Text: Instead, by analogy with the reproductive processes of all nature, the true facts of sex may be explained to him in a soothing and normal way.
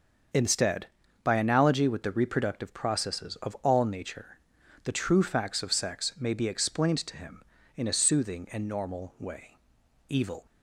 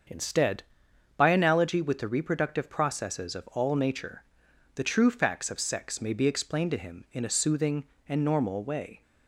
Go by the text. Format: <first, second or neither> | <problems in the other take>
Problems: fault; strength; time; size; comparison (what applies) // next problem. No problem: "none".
second | starts louder than the rest; until 1.7 s; 6.5 dB; also in the second // goes on to say "EVIL"; slight; from 10.0 s on; 0.38 s long